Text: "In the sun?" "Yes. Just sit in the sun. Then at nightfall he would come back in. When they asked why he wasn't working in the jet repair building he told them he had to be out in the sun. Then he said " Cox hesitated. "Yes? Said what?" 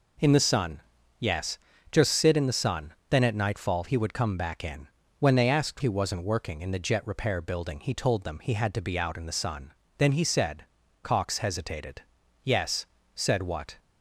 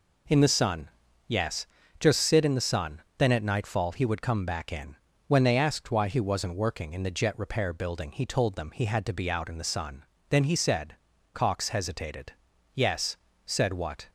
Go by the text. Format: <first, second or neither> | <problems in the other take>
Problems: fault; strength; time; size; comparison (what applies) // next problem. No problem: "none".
second | skips "why"; at 5.8 s